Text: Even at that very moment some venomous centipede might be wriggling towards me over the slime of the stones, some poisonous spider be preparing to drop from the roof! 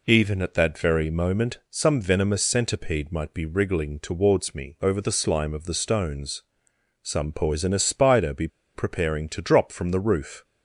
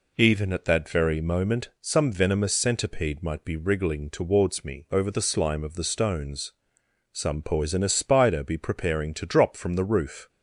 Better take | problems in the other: second | pauses between "be" and "preparing"; slight; at 8.4 s; 0.27 s long

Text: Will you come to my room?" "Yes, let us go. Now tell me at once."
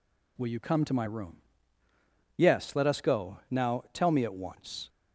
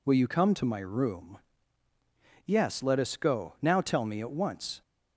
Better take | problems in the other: neither | none

